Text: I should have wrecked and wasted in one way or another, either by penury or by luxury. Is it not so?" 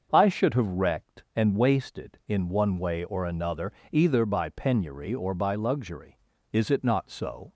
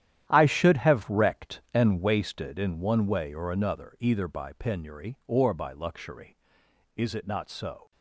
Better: first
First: starts louder than the rest; until 1.1 s; 6.5 dB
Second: gets quieter; strong; throughout; 14 dB // starts louder than the rest; strong; until 1.3 s; 11.5 dB

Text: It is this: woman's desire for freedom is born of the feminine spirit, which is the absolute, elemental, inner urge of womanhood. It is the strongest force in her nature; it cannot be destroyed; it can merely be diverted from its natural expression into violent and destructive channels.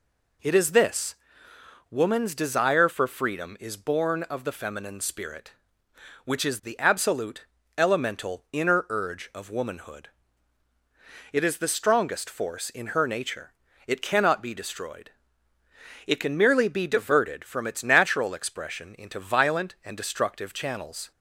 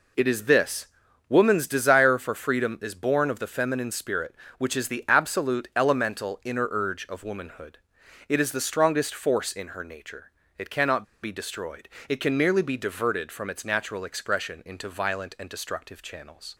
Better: first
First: none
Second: pauses between "cannot" and "be"; slight; at 11.0 s; 0.18 s long

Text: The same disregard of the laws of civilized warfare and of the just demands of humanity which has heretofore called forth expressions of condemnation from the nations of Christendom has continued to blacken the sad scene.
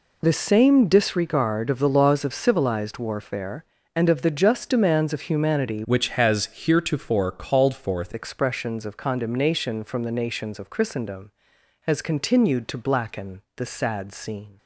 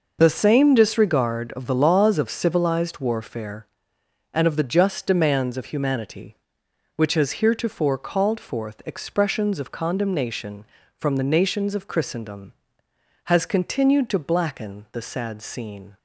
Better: second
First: changes voice from "which" to "forth"; from 5.8 to 8.1 s; 2.3 s long // pauses between "blacken" and "the"; slight; at 13.3 s; 0.16 s long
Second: none

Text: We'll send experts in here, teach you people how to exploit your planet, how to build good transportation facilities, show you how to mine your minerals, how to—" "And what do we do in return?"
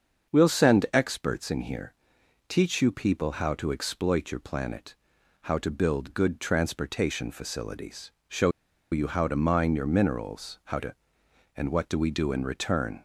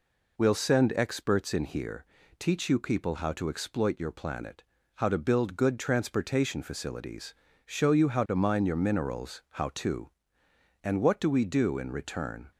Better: second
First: starts louder than the rest; until 1.3 s; 6.5 dB // pauses between "show" and "you"; at 8.4 s; 0.41 s long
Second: none

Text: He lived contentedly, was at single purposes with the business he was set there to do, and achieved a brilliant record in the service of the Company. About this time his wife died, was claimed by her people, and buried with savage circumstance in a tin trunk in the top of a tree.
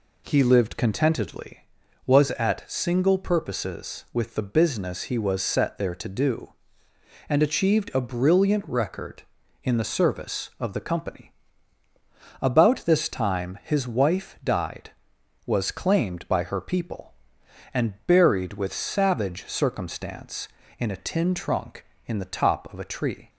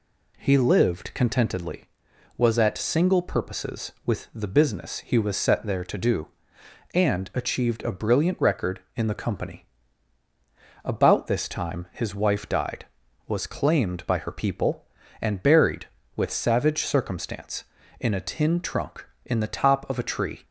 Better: first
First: none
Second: skips "the service of"; at 9.0 s

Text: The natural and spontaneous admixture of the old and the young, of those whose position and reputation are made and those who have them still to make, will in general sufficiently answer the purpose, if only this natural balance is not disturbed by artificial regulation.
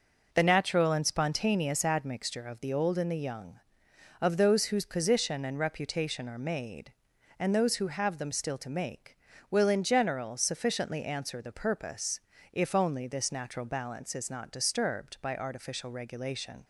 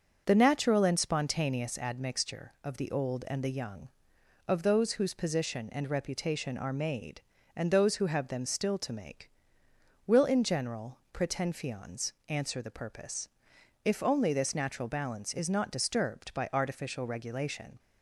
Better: first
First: none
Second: starts louder than the rest; until 1.2 s; 6.5 dB // says "pretenfions" for "sufficiently"; at 11.1 s

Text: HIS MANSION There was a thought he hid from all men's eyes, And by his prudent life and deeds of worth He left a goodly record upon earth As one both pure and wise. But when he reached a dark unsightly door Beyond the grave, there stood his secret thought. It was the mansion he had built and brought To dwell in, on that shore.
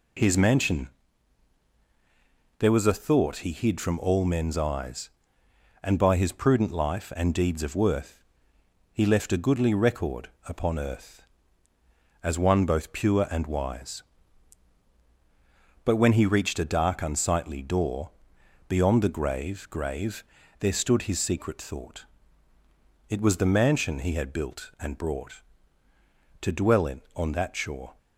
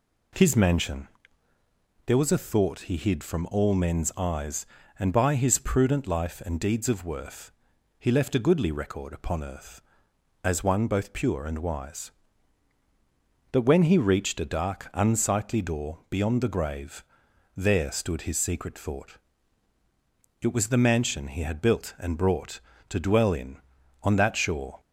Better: second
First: pauses between "MANSION" and "There"; strong; at 0.8 s; 1.6 s long // pauses between "worth" and "He"; noticeable; at 8.2 s; 0.68 s long // pauses between "record" and "upon"; slight; at 10.2 s; 0.18 s long // pauses between "door" and "Beyond"; noticeable; at 18.0 s; 0.58 s long // says "grave" twice; at 19.6 s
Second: pauses between "MANSION" and "There"; at 1.0 s; 1.0 s long // pauses between "worth" and "He"; noticeable; at 7.5 s; 0.48 s long

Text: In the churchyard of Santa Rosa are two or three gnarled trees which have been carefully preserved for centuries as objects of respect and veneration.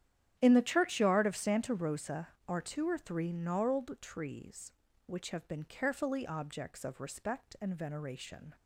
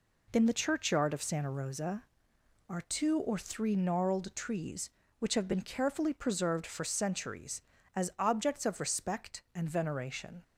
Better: second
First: starts louder than the rest; strong; until 1.4 s; 10.5 dB // skips "preserved for centuries as"; at 6.2 s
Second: none

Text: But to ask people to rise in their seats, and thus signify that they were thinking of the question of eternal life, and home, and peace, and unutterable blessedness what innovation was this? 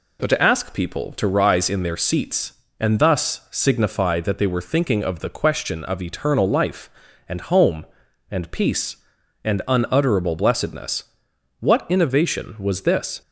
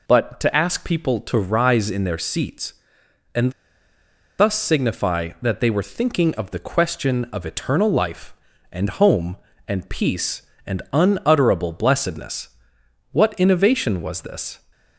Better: first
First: pauses between "blessedness" and "what"; noticeable; at 11.0 s; 0.54 s long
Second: pauses between "and" and "thus"; noticeable; at 3.5 s; 0.87 s long // pauses between "blessedness" and "what"; noticeable; at 12.4 s; 0.62 s long

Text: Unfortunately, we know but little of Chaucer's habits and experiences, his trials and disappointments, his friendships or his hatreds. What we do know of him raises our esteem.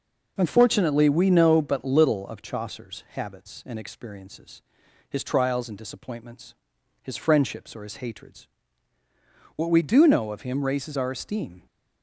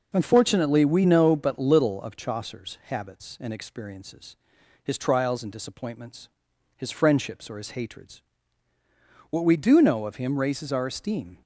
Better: neither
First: none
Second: none

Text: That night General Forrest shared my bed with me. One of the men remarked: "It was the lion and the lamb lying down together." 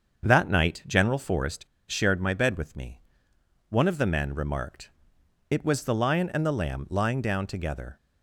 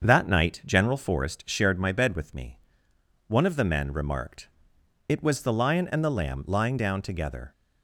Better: second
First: starts louder than the rest; until 1.2 s; 7 dB // pauses between "Forrest" and "shared"; slight; at 1.6 s; 0.23 s long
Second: starts louder than the rest; until 1.0 s; 7 dB

